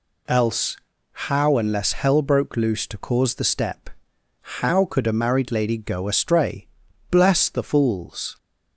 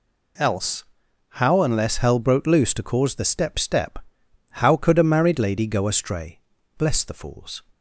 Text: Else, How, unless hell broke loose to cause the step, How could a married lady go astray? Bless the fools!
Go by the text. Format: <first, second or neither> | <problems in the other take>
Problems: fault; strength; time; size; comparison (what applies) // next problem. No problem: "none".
first | says "step" twice; at 3.5 s